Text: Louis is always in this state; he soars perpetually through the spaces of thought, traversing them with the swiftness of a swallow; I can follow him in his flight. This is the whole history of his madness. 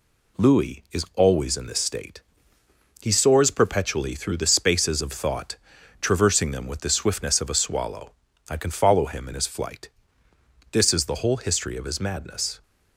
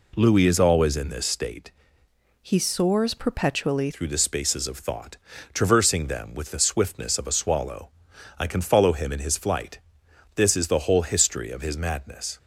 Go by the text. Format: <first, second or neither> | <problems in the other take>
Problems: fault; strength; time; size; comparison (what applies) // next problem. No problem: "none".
first | changes voice from "he" to "perpetually"; from 2.4 to 3.8 s; 1.4 s long